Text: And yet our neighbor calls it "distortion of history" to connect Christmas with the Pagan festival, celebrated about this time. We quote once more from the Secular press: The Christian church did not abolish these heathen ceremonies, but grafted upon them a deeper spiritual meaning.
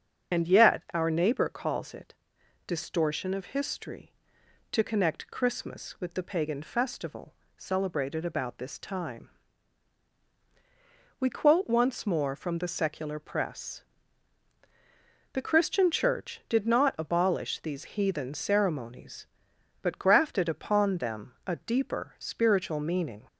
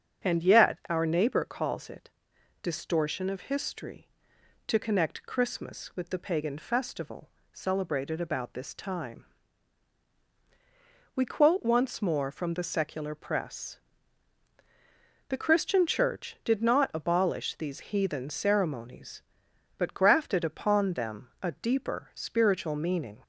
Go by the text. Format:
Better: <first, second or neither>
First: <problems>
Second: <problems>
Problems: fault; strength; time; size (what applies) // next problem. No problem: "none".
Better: second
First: loses the start of "And"; at 0.3 s; 45 ms // starts louder than the rest; strong; until 1.4 s; 7 dB // pauses between "it" and "distortion"; noticeable; at 2.1 s; 0.52 s long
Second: starts louder than the rest; strong; until 1.3 s; 7 dB // pauses between "it" and "distortion"; noticeable; at 2.0 s; 0.52 s long